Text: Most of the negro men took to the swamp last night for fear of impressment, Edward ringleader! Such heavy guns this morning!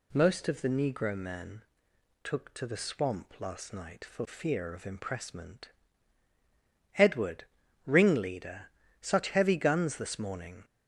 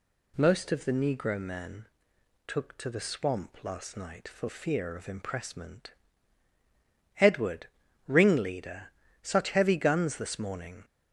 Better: neither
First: pauses between "men" and "took"; noticeable; at 1.6 s; 0.60 s long // pauses between "Edward" and "ringleader"; at 7.4 s; 0.42 s long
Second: pauses between "men" and "took"; noticeable; at 1.8 s; 0.60 s long // pauses between "Edward" and "ringleader"; at 7.6 s; 0.41 s long

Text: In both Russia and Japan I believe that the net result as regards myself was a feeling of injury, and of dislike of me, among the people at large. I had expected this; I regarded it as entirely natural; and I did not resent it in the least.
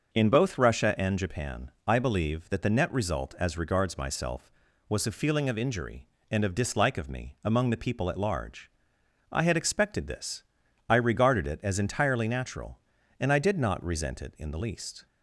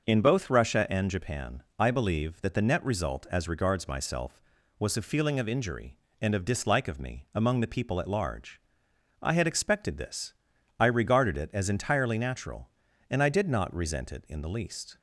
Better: neither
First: starts louder than the rest; noticeable; until 1.1 s; 6 dB // pauses between "Japan" and "I"; slight; at 1.7 s; 0.16 s long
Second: starts louder than the rest; noticeable; until 1.1 s; 6 dB // pauses between "Japan" and "I"; slight; at 1.6 s; 0.16 s long

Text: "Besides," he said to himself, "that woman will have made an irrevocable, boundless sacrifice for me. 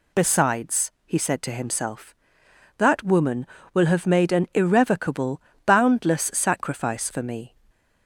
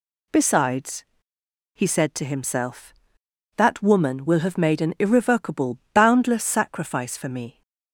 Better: neither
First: none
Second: none

